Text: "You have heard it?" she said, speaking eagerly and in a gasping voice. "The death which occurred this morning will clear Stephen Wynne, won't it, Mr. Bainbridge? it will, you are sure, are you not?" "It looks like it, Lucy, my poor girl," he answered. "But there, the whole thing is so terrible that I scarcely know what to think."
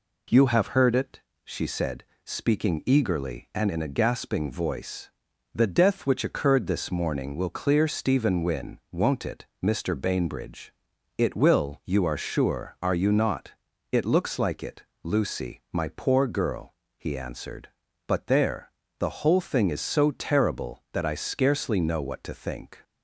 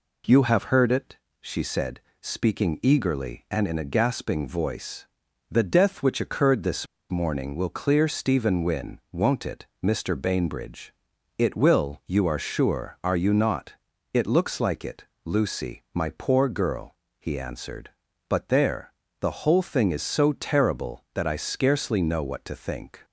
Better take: first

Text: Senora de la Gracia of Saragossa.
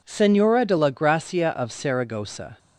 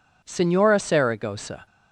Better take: first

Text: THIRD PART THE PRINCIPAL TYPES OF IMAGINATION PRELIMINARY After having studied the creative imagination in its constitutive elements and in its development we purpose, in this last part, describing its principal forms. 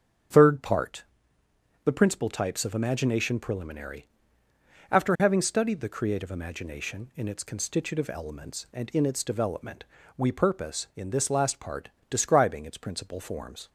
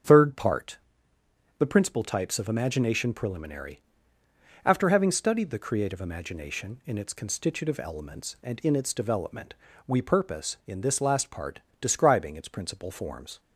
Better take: neither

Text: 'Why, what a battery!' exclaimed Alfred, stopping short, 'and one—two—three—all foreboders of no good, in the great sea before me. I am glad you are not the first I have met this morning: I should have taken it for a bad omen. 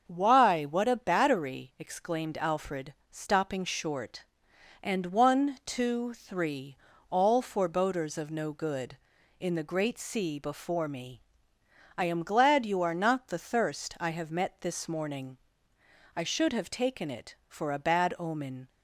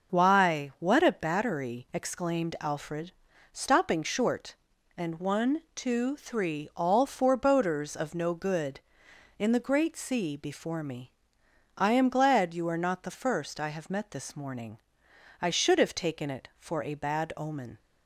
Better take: second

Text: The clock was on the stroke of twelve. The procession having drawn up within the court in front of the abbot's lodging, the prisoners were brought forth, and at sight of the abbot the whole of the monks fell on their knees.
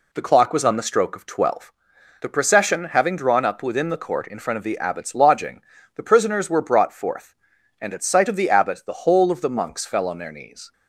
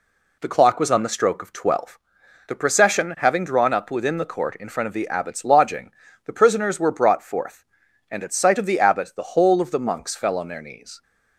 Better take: neither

